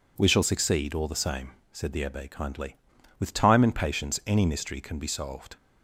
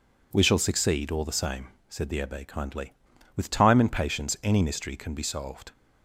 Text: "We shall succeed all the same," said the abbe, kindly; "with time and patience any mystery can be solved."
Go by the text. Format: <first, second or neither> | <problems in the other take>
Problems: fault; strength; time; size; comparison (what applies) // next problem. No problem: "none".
neither | none